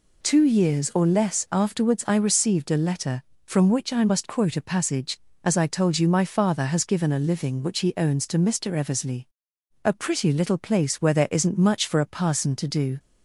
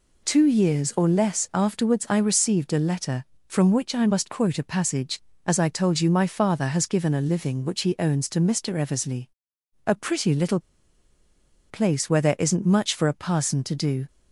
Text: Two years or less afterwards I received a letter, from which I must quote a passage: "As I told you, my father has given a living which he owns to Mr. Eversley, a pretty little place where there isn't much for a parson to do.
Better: first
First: none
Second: pauses between "little" and "place"; at 10.6 s; 1.0 s long

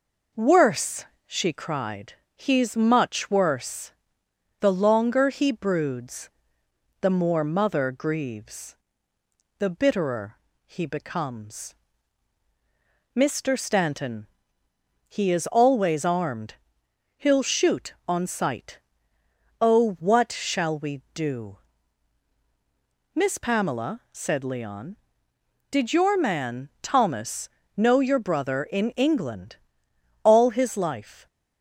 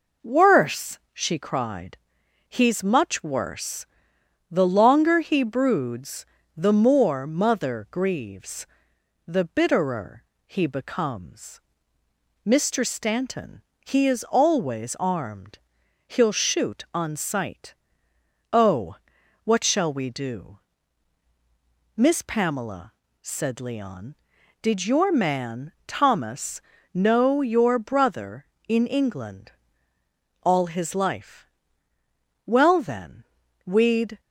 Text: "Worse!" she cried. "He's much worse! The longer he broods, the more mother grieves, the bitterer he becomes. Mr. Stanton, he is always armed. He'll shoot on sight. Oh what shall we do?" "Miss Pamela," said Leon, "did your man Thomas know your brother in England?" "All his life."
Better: first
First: pauses between "bitterer" and "he"; slight; at 10.3 s; 0.28 s long // pauses between "Thomas" and "know"; slight; at 27.5 s; 0.26 s long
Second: pauses between "bitterer" and "he"; slight; at 10.2 s; 0.22 s long // pauses between "Oh" and "what"; noticeable; at 18.9 s; 0.48 s long // pauses between "Thomas" and "know"; slight; at 26.5 s; 0.32 s long // goes on to say "Well then we'd"; strong; from 32.4 s on; 1.7 s long

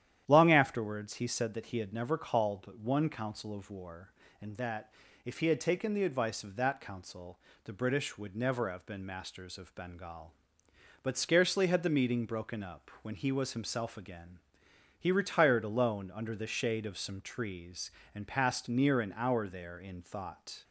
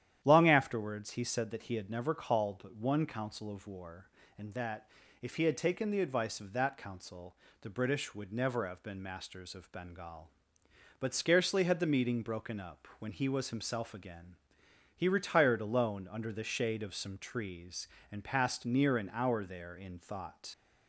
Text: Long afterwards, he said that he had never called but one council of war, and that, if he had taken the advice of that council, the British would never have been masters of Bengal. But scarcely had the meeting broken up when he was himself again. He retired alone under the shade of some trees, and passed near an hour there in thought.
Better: first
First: starts louder than the rest; strong; until 1.2 s; 10.5 dB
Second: starts louder than the rest; strong; until 1.2 s; 10.5 dB // leaves "thought" unfinished; at 20.5 s; 60 ms

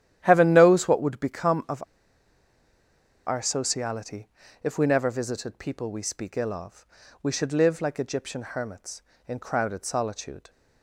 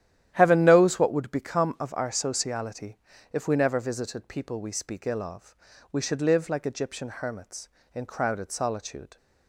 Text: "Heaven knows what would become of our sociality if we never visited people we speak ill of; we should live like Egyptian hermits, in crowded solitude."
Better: second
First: starts louder than the rest; strong; until 1.2 s; 11.5 dB // pauses between "of" and "our"; strong; at 1.8 s; 1.4 s long // pauses between "sociality" and "if"; slight; at 4.2 s; 0.36 s long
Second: starts louder than the rest; strong; until 1.3 s; 11.5 dB // pauses between "sociality" and "if"; slight; at 2.9 s; 0.36 s long

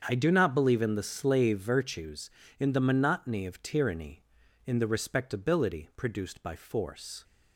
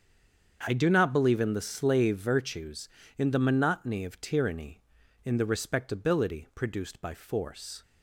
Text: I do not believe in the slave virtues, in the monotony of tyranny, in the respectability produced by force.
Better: first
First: starts louder than the rest; strong; until 1.0 s; 7 dB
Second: stays silent before the first word; slight; until 0.6 s; 0.6 s long // starts louder than the rest; strong; until 1.6 s; 7 dB

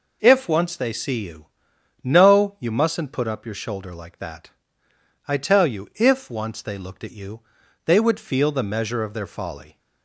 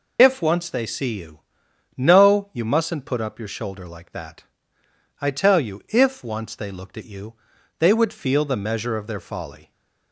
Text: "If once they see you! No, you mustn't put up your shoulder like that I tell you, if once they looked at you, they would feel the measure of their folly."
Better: first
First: pauses between "that" and "I"; noticeable; at 4.4 s; 0.78 s long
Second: loses the start of "If"; at 0.1 s; 45 ms // pauses between "that" and "I"; noticeable; at 4.4 s; 0.78 s long

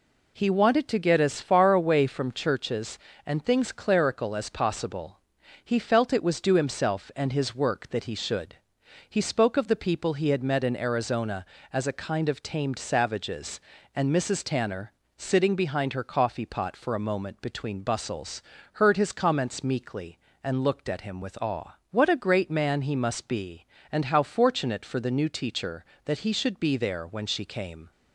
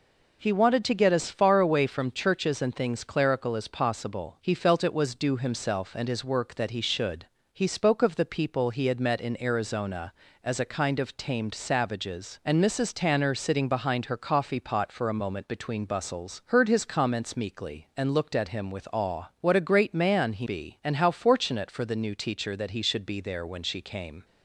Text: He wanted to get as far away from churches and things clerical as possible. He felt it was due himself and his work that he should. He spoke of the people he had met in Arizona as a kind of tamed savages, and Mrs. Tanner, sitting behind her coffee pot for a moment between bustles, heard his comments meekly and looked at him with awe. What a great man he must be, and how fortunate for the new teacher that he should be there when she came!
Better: first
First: none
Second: skips "must"; at 20.4 s

